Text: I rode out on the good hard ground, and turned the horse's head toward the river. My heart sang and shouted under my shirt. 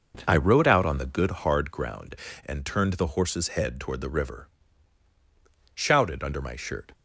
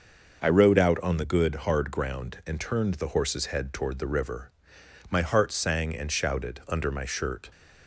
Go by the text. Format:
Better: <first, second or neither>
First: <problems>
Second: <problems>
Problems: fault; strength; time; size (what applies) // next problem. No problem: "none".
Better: second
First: skips "My heart sang and"; at 5.1 s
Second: none